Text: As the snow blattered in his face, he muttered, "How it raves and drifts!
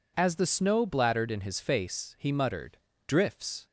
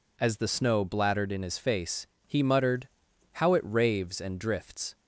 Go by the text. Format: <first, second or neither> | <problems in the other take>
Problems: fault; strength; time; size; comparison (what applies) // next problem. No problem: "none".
second | skips "How it raves and"; at 2.9 s